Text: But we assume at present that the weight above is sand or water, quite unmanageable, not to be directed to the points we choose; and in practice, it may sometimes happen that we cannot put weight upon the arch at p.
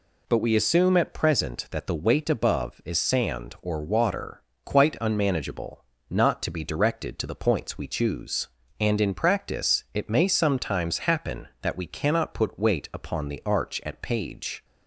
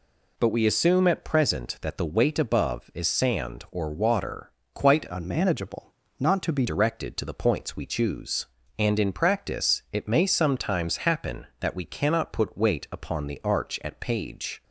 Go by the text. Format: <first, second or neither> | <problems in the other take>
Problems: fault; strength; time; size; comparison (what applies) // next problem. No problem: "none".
first | changes voice from "unmanageable" to "be"; from 5.0 to 6.6 s; 1.6 s long